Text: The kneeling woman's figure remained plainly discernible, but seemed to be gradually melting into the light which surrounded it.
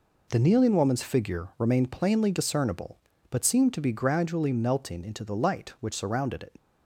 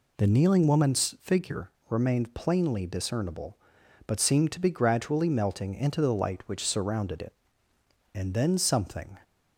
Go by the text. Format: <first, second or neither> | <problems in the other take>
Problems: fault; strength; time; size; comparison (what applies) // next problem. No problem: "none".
first | pauses between "figure" and "remained"; slight; at 1.7 s; 0.18 s long // goes on to say "And then something"; noticeable; from 8.1 s on; 1.0 s long